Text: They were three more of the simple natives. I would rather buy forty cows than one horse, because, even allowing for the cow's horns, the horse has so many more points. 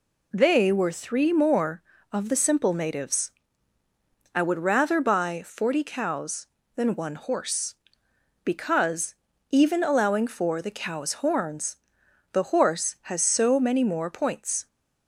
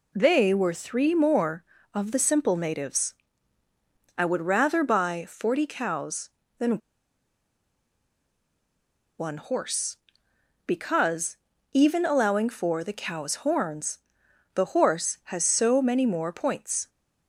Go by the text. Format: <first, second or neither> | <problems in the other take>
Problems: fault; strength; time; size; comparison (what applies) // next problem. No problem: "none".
first | pauses between "than" and "one"; strong; at 6.7 s; 2.3 s long